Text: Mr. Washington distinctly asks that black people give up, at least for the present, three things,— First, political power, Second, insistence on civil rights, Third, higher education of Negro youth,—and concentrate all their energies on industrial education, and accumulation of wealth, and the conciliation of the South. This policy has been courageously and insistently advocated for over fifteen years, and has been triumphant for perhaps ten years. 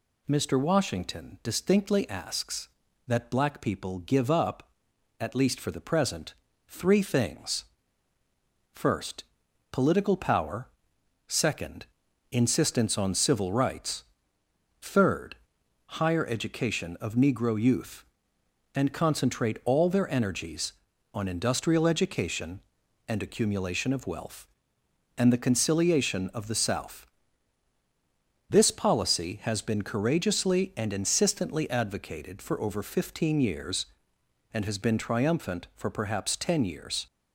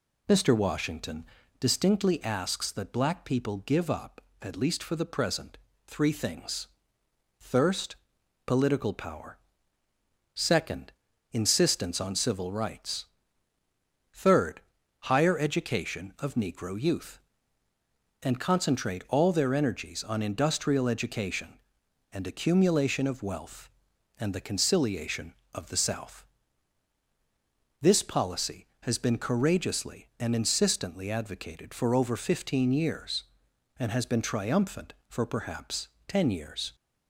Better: first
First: none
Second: pauses between "Washington" and "distinctly"; slight; at 1.2 s; 0.34 s long // says "Thirst" for "First"; at 7.4 s // pauses between "perhaps" and "ten"; slight; at 35.8 s; 0.18 s long

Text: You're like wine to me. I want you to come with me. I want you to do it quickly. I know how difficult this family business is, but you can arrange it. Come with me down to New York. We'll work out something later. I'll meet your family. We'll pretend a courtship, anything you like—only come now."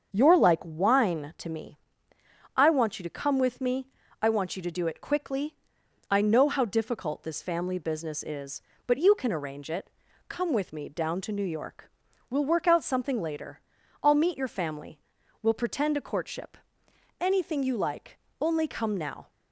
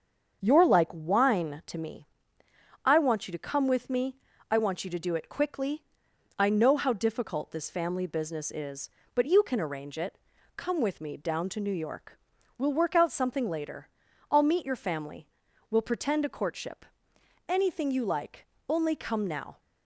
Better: neither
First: starts louder than the rest; until 1.1 s; 7 dB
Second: starts louder than the rest; until 1.4 s; 7 dB

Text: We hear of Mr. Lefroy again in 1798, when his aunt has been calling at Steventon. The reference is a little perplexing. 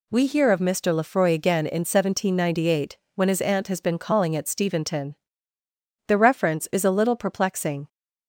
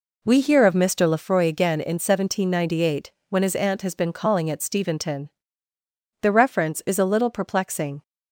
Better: first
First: none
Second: starts louder than the rest; until 1.3 s; 3.5 dB

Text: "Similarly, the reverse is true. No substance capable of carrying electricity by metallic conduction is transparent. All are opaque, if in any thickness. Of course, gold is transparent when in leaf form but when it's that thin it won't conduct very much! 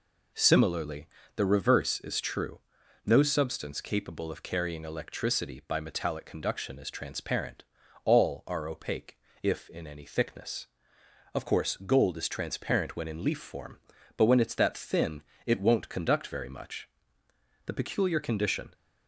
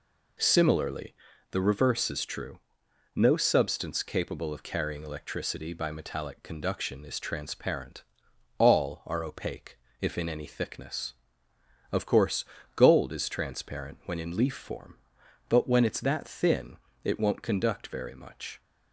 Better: second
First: pauses between "thin" and "it"; slight; at 15.2 s; 0.24 s long // goes on to say "The peculiar condition"; noticeable; from 17.6 s on; 1.0 s long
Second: pauses between "thin" and "it"; slight; at 16.7 s; 0.26 s long

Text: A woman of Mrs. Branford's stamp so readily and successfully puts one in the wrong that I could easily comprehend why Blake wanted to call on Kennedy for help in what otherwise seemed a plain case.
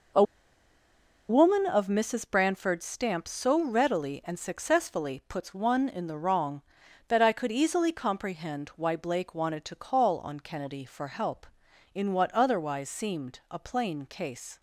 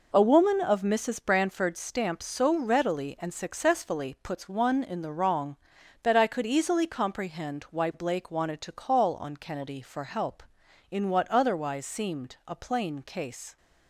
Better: second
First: pauses between "A" and "woman"; at 0.2 s; 1.0 s long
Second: none

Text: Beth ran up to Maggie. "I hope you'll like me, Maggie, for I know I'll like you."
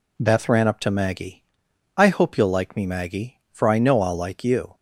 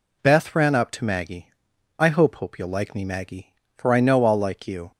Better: first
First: none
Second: says "hope" twice; at 2.3 s

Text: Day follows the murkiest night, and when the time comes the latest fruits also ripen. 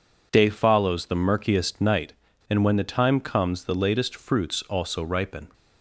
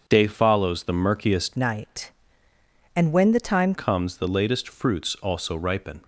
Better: first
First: none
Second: starts louder than the rest; until 1.0 s; 7 dB // changes voice from "night" to "time"; from 1.5 to 3.7 s; 2.2 s long

